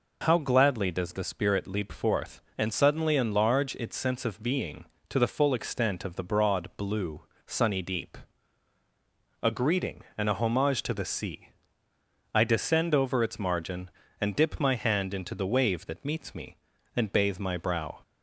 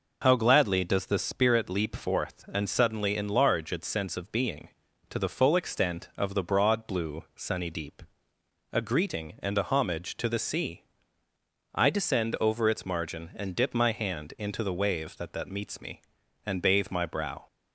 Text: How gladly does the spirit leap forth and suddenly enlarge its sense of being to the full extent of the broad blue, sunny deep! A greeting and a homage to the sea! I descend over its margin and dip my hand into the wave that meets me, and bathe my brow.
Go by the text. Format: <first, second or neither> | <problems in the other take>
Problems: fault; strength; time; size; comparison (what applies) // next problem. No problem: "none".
first | says "that" twice; at 15.3 s